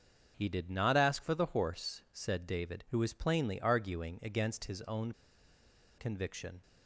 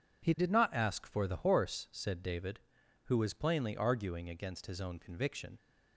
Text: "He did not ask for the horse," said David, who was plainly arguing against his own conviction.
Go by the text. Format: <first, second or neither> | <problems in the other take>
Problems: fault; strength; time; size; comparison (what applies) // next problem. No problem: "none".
second | starts louder than the rest; until 1.3 s; 6.5 dB // pauses between "own" and "conviction"; noticeable; at 5.1 s; 0.85 s long